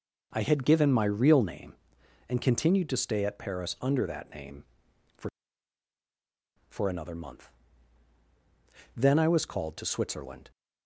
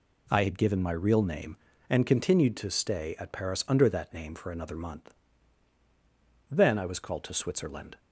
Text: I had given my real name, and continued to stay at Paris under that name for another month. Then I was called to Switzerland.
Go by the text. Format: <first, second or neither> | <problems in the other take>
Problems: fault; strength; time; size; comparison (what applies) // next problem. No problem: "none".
second | says "for" twice; at 6.6 s